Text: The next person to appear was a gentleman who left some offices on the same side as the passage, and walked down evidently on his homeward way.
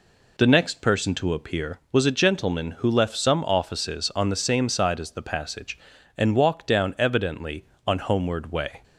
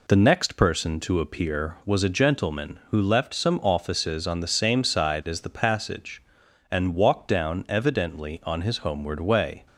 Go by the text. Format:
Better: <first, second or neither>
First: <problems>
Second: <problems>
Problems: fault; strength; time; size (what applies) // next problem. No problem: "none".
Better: second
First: skips "his"; at 7.9 s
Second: none